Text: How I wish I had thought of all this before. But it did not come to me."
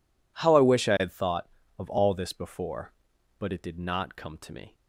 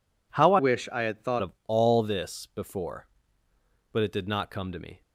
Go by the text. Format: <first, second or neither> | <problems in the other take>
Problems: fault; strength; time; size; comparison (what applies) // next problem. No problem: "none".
first | changes voice from "wish" to "thought"; from 0.5 to 1.4 s; 0.9 s long